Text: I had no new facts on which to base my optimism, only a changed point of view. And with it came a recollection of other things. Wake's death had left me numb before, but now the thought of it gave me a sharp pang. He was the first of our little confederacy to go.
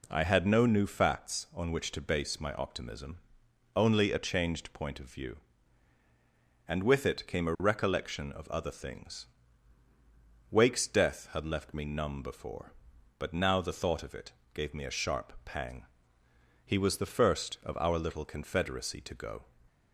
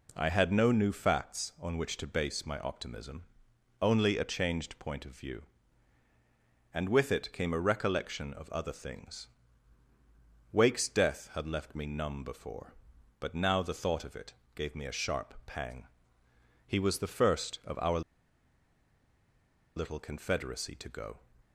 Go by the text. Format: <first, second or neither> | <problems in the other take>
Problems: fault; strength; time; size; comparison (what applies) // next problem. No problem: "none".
first | pauses between "it" and "gave"; slight; at 14.3 s; 0.20 s long; slight in the first // pauses between "our" and "little"; strong; at 18.0 s; 1.7 s long